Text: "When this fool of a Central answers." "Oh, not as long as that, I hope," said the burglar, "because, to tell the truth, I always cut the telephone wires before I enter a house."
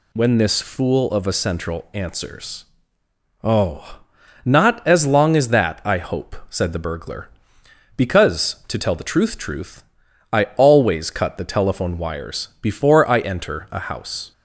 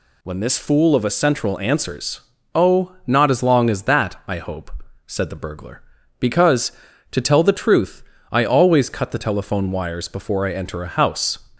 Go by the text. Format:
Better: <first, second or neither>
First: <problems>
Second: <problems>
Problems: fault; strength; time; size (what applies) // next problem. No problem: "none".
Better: second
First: says "truth" twice; at 9.3 s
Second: none